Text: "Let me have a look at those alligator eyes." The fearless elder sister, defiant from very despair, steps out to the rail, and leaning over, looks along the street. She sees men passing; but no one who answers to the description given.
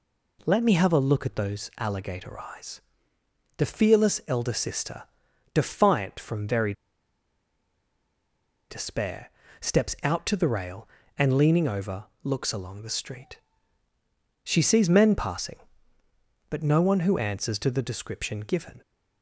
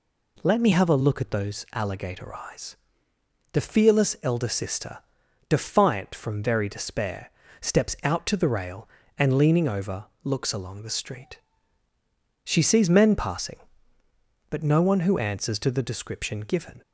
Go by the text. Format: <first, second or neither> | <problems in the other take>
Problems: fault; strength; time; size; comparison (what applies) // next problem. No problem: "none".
second | pauses between "very" and "despair"; strong; at 6.7 s; 1.9 s long